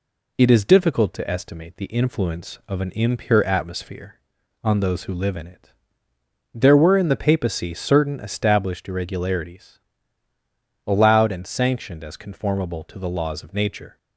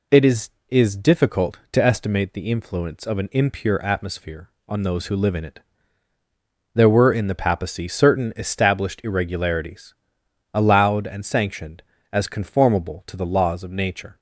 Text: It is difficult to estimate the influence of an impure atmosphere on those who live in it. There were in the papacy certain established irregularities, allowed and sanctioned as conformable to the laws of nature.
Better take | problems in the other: first | says "is" twice; at 0.6 s

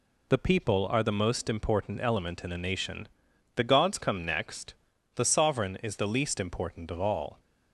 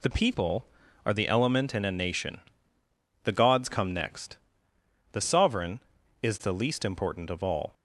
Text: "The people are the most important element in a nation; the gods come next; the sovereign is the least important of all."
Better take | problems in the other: first | skips "most important"; at 1.2 s

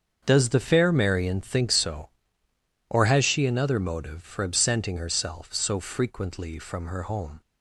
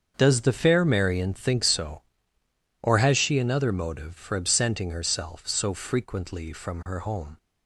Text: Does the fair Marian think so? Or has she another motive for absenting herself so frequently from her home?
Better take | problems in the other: neither | starts louder than the rest; the same in both

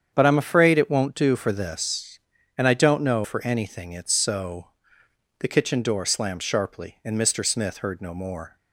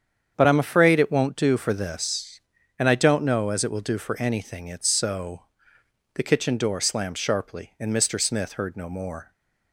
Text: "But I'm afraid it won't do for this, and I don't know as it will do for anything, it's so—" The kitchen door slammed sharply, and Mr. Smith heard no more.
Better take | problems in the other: second | starts louder than the rest; strong; until 1.1 s; 8 dB; strong in the second // skips "as it will do"; at 3.2 s

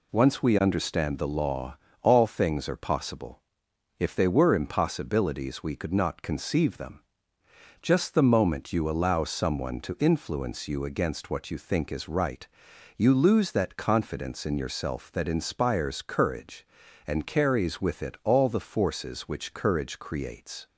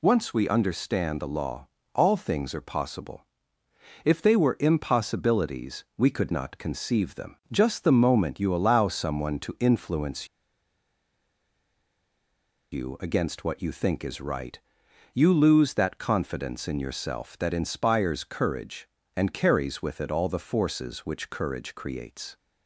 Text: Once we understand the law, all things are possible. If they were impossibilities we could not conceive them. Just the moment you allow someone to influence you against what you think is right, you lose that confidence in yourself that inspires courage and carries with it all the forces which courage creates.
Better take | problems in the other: first | pauses between "influence" and "you"; strong; at 10.2 s; 2.4 s long

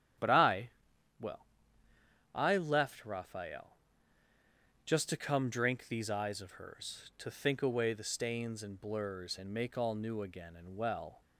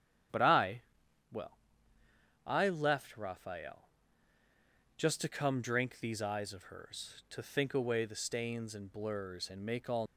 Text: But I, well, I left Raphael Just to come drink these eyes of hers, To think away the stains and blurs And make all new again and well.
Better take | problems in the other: first | starts louder than the rest; strong; until 2.7 s; 10 dB; strong in the first // pauses between "Raphael" and "Just"; at 3.8 s; 1.0 s long; also in the first // stops before "new again and well"; at 10.0 s

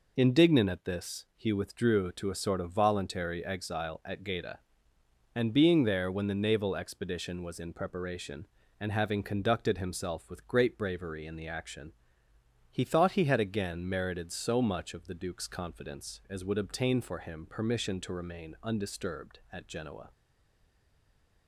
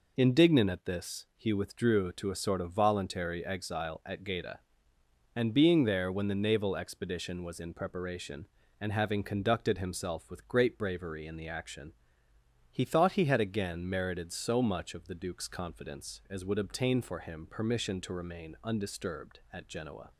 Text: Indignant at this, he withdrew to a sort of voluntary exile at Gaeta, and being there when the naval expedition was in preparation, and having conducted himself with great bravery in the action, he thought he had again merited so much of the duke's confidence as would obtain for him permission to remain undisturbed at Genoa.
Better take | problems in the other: second | stays silent after the last word; noticeable; from 20.1 s on; 1.3 s long

